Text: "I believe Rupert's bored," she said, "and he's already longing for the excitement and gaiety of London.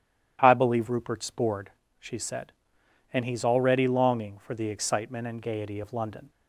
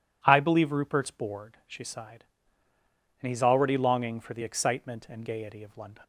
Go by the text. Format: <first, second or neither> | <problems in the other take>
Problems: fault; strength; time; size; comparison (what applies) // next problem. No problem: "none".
first | says "sighed" for "said"; at 1.8 s